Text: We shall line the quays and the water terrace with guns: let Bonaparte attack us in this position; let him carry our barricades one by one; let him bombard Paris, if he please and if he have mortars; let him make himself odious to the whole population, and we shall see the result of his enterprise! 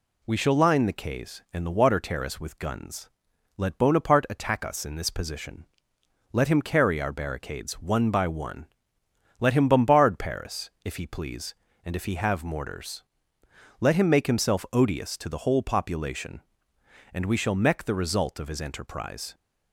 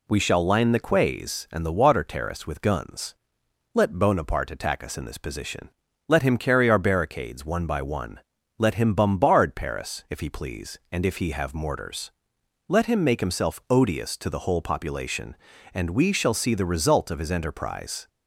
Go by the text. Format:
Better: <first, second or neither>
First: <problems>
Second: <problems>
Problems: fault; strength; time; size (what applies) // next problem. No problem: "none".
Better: second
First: says "mech" for "see"; at 17.5 s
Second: none